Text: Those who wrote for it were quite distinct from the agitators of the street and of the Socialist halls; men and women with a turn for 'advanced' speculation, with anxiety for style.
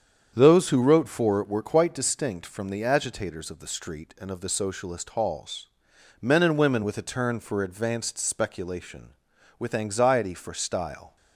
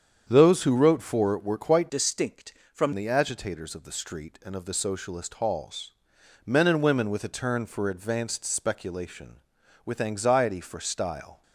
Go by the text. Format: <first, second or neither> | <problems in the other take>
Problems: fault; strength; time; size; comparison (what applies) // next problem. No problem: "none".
first | starts louder than the rest; strong; until 1.2 s; 8 dB; strong in the first // changes voice from "distinct" to "from"; from 1.8 to 2.9 s; 1.1 s long